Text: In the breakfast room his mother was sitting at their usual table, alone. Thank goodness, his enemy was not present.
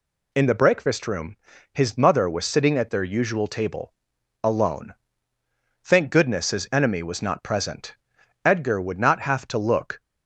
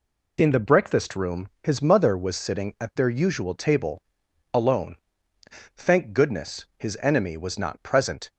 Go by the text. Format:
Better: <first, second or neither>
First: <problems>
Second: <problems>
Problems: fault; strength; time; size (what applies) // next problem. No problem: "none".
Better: second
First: pauses between "room" and "his"; at 1.3 s; 0.38 s long // goes on to say "Edgar would not have to look"; from 8.4 s on; 1.5 s long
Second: none